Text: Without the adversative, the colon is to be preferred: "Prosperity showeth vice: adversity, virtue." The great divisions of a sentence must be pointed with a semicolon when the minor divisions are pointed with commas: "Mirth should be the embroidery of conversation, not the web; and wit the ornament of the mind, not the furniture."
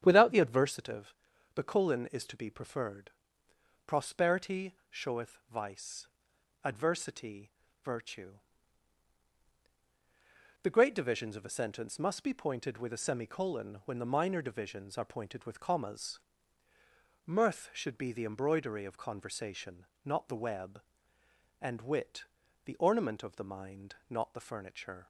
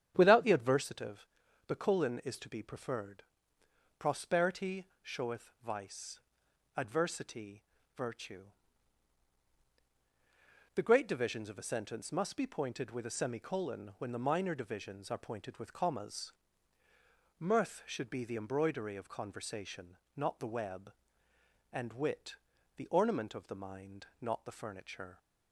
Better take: neither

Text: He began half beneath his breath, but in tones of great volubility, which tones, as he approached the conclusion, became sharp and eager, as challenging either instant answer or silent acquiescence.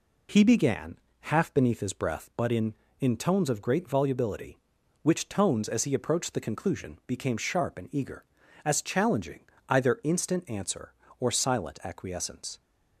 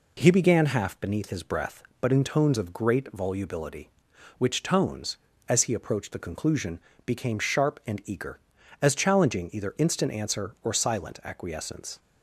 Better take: second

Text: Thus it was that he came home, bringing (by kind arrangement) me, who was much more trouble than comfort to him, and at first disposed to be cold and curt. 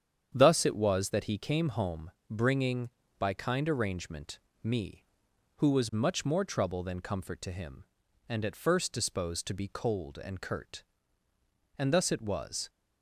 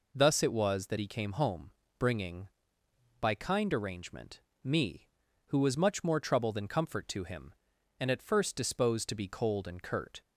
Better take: second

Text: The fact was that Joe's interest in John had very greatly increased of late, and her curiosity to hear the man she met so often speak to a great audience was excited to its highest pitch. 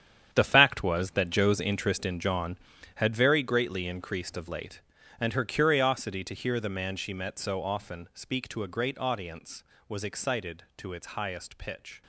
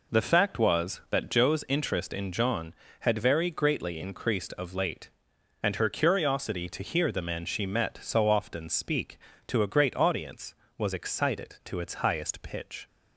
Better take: second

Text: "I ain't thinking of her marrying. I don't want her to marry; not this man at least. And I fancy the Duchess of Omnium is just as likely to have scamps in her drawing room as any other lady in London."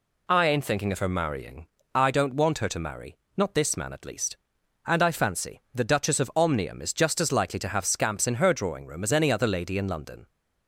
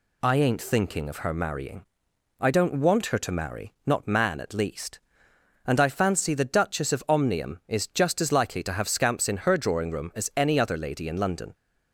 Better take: first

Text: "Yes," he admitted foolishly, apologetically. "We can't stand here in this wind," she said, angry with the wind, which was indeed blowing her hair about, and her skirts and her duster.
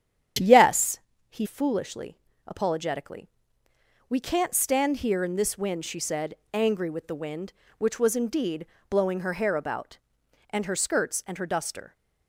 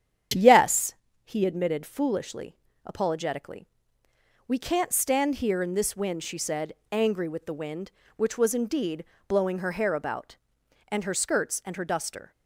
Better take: second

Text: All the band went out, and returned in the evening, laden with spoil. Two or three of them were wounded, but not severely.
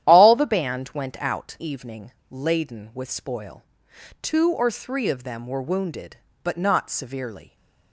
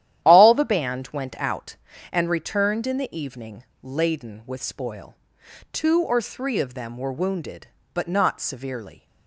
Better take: second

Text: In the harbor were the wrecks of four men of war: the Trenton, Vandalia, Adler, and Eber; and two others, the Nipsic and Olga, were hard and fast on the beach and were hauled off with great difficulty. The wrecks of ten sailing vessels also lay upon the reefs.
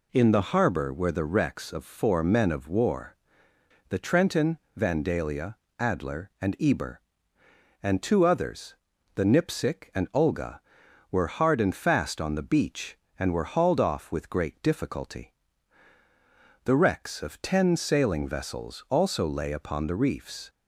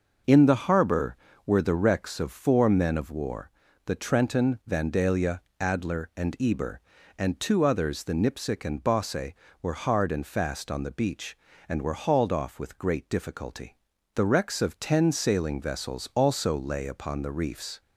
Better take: first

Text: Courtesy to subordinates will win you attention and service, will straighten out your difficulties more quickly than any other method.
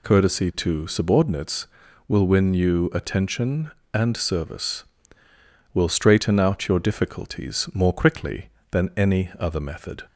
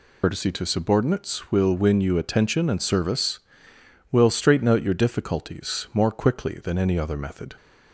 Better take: first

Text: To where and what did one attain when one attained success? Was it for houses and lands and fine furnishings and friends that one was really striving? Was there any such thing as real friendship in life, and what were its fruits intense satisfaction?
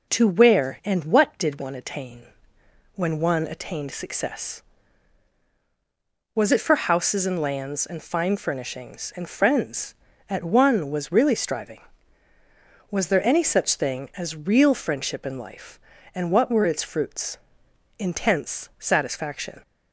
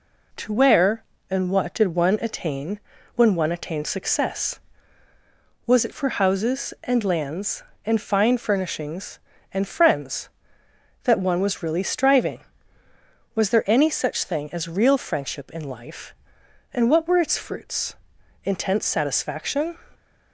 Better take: second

